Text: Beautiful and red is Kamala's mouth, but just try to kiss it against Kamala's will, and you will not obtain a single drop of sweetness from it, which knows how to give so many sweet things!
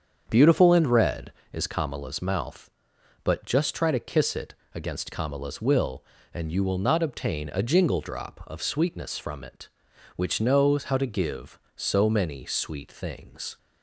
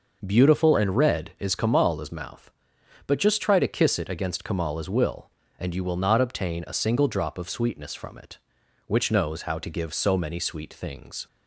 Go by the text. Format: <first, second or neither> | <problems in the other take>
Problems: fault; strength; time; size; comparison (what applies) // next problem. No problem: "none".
second | starts louder than the rest; strong; until 1.2 s; 7.5 dB // pauses between "it" and "against"; slight; at 4.5 s; 0.18 s long // says "jingle" for "single"; at 7.6 s